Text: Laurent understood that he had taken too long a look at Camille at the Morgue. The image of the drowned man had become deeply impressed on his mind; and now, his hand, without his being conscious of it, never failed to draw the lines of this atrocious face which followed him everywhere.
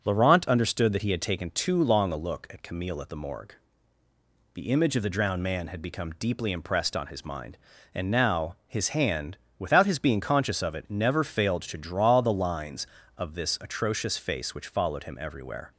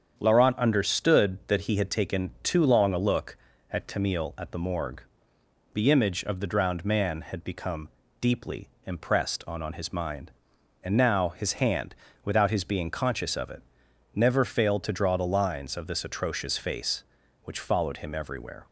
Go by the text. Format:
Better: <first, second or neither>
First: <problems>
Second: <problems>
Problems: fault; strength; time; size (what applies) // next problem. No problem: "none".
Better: first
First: none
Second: starts louder than the rest; strong; until 1.1 s; 8 dB // pauses between "become" and "deeply"; slight; at 7.8 s; 0.32 s long // pauses between "deeply" and "impressed"; slight; at 8.6 s; 0.18 s long // says "on" twice; at 9.6 s